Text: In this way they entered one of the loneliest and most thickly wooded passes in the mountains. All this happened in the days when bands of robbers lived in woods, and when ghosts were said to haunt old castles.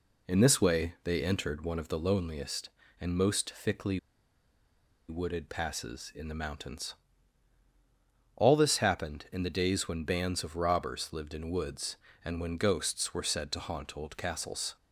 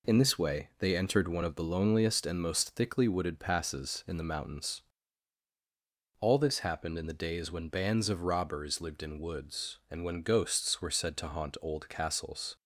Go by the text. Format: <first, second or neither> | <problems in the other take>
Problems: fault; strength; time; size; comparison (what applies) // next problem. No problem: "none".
second | pauses between "thickly" and "wooded"; at 3.9 s; 1.0 s long